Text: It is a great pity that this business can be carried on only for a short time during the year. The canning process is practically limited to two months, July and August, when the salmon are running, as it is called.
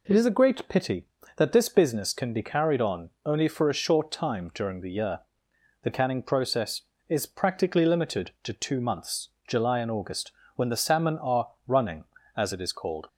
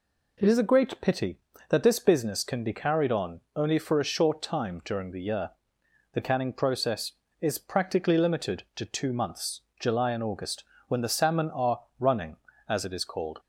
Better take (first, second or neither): neither